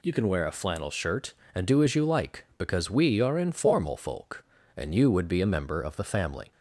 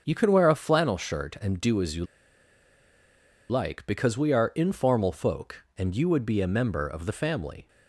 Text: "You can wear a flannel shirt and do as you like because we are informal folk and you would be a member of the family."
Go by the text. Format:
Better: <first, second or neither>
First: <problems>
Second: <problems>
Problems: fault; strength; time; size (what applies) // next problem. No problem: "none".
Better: first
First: none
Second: starts louder than the rest; until 1.0 s; 7 dB // pauses between "you" and "like"; strong; at 2.0 s; 1.4 s long